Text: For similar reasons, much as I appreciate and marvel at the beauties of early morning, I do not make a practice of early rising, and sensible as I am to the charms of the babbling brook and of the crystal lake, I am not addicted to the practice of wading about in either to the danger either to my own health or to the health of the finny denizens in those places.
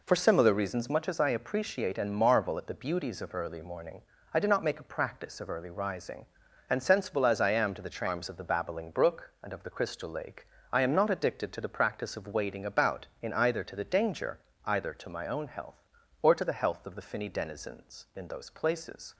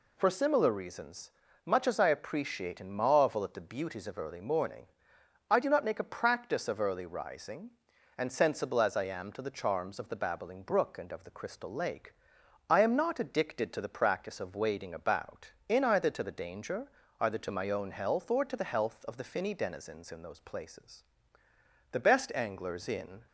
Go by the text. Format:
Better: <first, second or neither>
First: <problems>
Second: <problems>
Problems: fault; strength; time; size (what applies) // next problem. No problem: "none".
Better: first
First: pauses between "danger" and "either"; slight; at 14.3 s; 0.26 s long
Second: pauses between "danger" and "either"; slight; at 16.8 s; 0.32 s long // goes on to say "The best anglers in"; from 21.9 s on; 1.3 s long